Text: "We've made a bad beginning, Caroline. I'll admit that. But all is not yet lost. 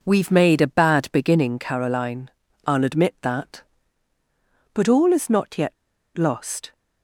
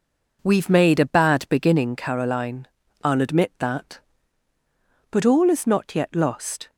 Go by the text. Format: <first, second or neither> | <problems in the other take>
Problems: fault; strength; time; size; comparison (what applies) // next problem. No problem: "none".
second | pauses between "yet" and "lost"; at 5.7 s; 0.41 s long